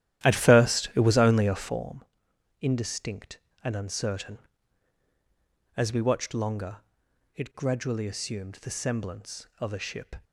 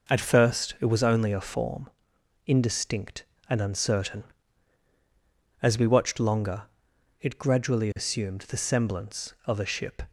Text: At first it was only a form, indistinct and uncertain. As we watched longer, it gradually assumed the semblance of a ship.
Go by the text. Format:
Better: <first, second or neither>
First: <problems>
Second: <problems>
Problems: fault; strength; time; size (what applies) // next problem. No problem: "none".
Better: second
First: starts louder than the rest; strong; until 1.8 s; 12.5 dB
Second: none